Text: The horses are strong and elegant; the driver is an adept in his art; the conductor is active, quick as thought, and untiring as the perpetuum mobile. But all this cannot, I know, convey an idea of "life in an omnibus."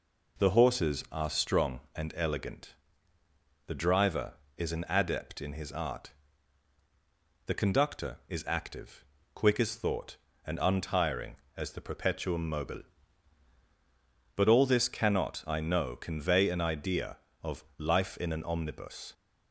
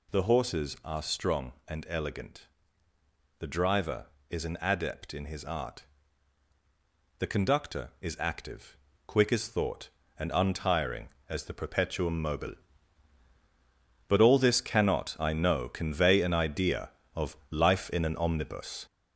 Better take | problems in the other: first | gets louder; noticeable; throughout; 5 dB // pauses between "of" and "life"; slight; at 17.3 s; 0.16 s long; slight in the first

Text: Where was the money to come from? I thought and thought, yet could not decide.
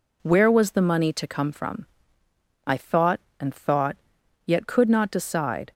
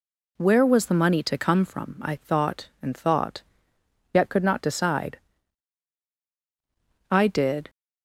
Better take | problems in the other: first | goes on to say "I did"; from 7.1 s on; 0.58 s long

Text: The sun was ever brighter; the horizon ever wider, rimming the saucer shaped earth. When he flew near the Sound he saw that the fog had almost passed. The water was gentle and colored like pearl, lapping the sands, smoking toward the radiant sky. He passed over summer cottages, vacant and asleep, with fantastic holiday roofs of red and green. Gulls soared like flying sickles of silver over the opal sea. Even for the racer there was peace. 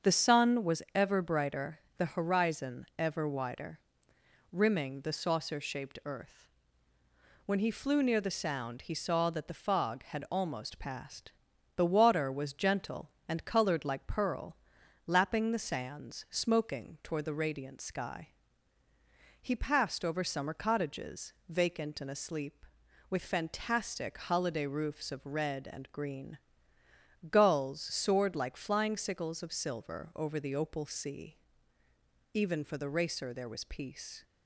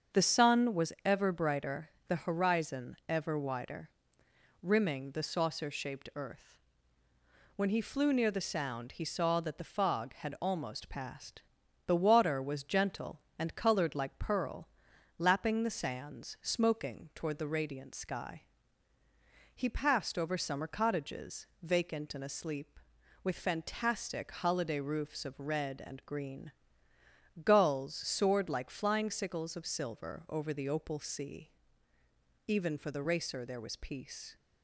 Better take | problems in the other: neither | starts louder than the rest; strong; the same in both

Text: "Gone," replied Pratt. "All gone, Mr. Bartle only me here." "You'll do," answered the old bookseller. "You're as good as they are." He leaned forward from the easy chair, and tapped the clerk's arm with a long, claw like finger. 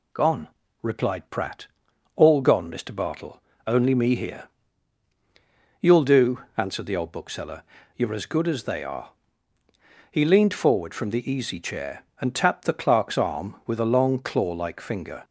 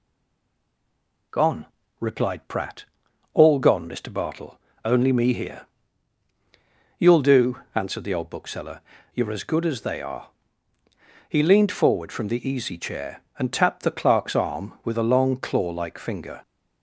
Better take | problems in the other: first | stays silent before the first word; noticeable; until 1.3 s; 1.3 s long // pauses between "Bartle" and "only"; slight; at 4.5 s; 0.24 s long; slight in the first

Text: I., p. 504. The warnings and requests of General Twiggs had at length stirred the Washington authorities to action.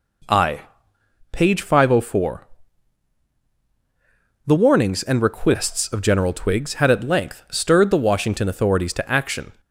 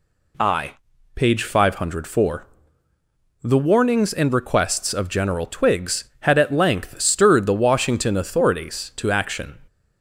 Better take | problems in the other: second | starts louder than the rest; until 1.3 s; 4 dB

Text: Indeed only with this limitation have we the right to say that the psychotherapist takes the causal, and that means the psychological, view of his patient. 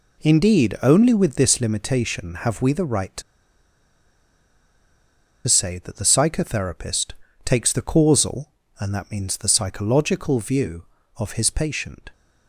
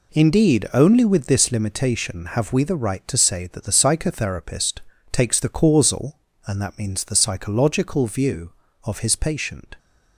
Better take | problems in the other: second | pauses between "to" and "say"; strong; at 3.2 s; 2.2 s long // pauses between "psychotherapist" and "takes"; slight; at 7.1 s; 0.32 s long; slight in the second

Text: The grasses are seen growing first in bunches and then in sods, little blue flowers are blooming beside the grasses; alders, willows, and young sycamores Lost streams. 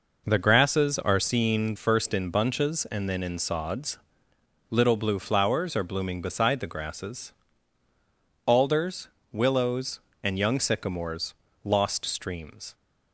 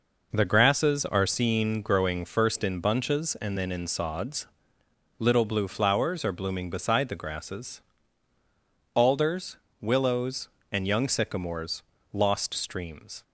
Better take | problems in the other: second | skips "growing"; at 1.7 s // pauses between "sycamores" and "Lost"; slight; at 11.3 s; 0.32 s long; slight in the second

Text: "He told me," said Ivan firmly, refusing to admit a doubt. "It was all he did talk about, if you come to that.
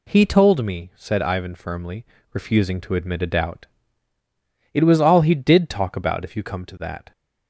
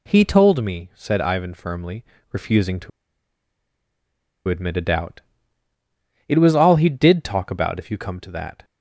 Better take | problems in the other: first | pauses between "to" and "admit"; strong; at 2.9 s; 1.5 s long

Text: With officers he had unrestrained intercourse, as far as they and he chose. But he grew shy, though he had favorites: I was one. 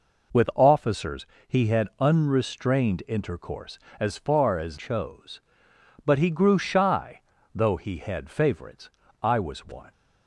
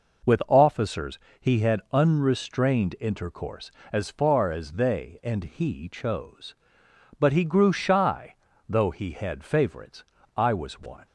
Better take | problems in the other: second | pauses between "officers" and "he"; slight; at 1.2 s; 0.22 s long; slight in the second // skips "they and he"; at 4.7 s

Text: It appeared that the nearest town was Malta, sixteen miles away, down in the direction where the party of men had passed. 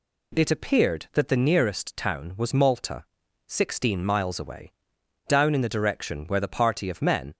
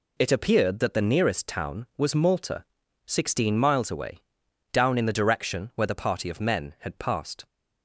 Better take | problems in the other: second | stops before "had passed"; at 7.3 s

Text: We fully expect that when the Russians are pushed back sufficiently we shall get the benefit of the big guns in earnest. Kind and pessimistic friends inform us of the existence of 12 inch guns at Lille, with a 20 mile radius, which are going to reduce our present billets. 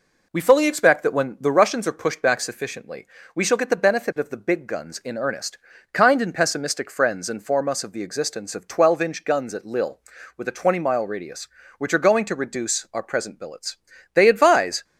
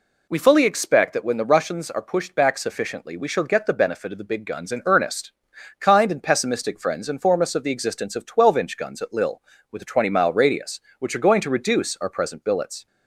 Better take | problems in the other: second | pauses between "sufficiently" and "we"; slight; at 3.0 s; 0.28 s long // goes on to say "They advise"; noticeable; from 14.1 s on; 0.70 s long

